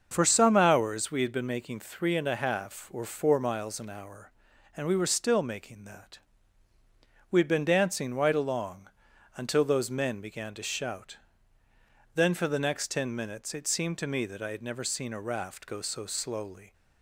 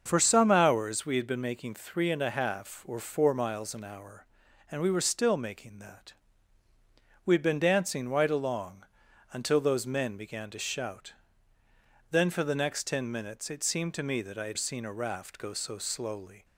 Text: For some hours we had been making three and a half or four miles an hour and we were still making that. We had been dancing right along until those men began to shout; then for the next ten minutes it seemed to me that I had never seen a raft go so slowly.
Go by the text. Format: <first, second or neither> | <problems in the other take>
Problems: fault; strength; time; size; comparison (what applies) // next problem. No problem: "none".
first | starts louder than the rest; until 1.0 s; 6.5 dB; also in the first // pauses between "along" and "until"; noticeable; at 8.8 s; 0.48 s long; noticeable in the first // skips "never"; at 14.5 s